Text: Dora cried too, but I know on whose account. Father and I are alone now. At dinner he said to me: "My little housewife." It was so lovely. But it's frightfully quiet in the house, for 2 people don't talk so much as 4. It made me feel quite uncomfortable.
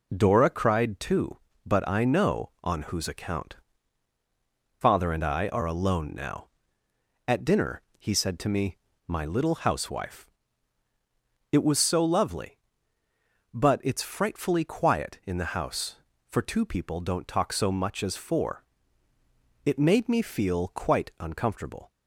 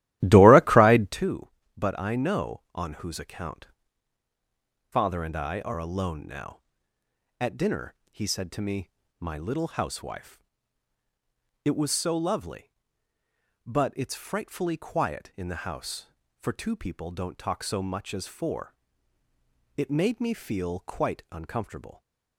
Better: first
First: pauses between "dinner" and "he"; slight; at 7.8 s; 0.16 s long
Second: starts louder than the rest; strong; until 1.3 s; 14.5 dB // pauses between "dinner" and "he"; slight; at 7.9 s; 0.16 s long

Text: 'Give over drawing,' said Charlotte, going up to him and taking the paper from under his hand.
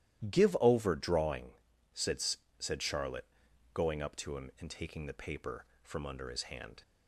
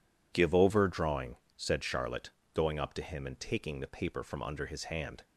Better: second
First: says "said" twice; at 2.5 s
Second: none

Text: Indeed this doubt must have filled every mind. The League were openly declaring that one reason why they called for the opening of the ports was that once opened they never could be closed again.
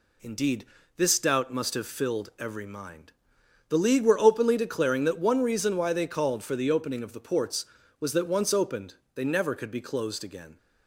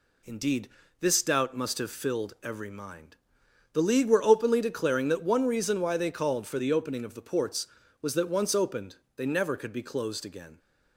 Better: neither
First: pauses between "Indeed" and "this"; slight; at 0.6 s; 0.30 s long // pauses between "opened" and "they"; slight; at 8.9 s; 0.20 s long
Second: pauses between "Indeed" and "this"; slight; at 0.6 s; 0.30 s long // pauses between "opened" and "they"; slight; at 8.9 s; 0.20 s long

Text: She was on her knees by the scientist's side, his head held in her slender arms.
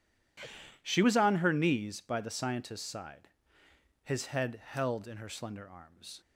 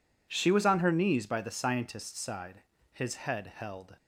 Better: first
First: none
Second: stops before "in her slender arms"; at 3.9 s

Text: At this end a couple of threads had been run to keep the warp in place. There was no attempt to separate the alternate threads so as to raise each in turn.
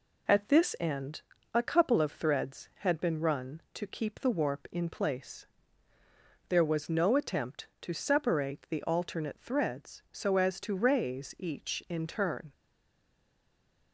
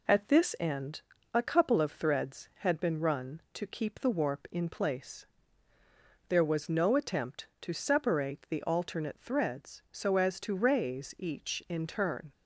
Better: second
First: pauses between "end" and "a"; slight; at 1.2 s; 0.32 s long // stays silent after the last word; noticeable; from 12.5 s on; 1.4 s long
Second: pauses between "end" and "a"; slight; at 1.0 s; 0.32 s long

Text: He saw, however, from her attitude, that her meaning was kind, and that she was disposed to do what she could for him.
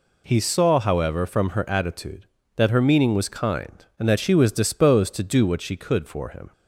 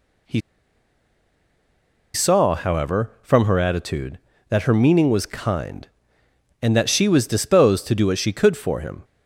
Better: first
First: none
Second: pauses between "He" and "saw"; strong; at 0.4 s; 1.7 s long

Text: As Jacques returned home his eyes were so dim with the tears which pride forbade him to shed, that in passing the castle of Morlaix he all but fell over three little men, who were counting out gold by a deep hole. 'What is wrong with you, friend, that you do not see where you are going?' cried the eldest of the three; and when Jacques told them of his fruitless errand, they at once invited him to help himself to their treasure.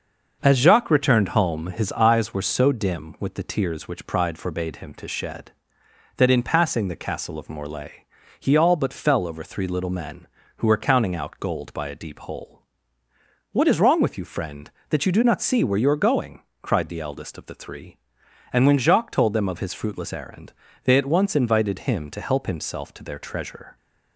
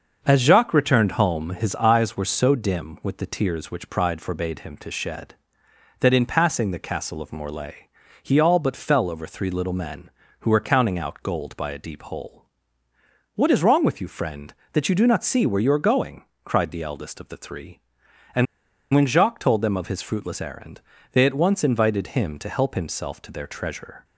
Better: first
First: starts louder than the rest; until 1.4 s; 6 dB // pauses between "Morlaix" and "he"; slight; at 8.0 s; 0.34 s long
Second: starts louder than the rest; until 1.2 s; 6 dB // pauses between "Morlaix" and "he"; slight; at 7.8 s; 0.34 s long // pauses between "and" and "when"; noticeable; at 18.4 s; 0.48 s long

